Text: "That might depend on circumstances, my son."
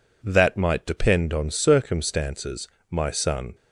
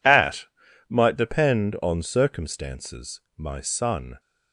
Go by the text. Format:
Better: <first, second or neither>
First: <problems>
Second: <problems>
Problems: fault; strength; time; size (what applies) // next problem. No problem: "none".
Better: first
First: none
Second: says "At" for "That"; at 0.0 s